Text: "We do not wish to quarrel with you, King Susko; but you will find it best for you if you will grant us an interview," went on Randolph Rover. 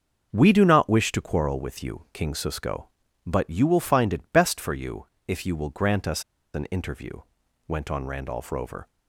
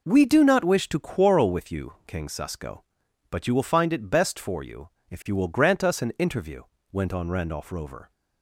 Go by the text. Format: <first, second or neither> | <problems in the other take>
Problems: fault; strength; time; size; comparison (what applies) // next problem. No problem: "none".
second | starts louder than the rest; until 1.3 s; 6.5 dB // pauses between "you" and "if"; slight; at 5.0 s; 0.20 s long; slight in the second // pauses between "us" and "an"; slight; at 6.2 s; 0.32 s long